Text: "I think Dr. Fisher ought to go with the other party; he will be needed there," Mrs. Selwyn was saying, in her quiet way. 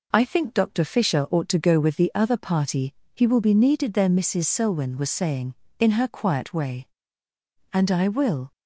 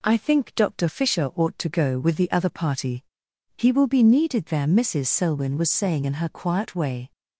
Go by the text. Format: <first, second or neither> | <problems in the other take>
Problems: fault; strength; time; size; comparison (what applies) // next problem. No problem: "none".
second | goes on to say "And I will"; noticeable; from 7.7 s on; 0.78 s long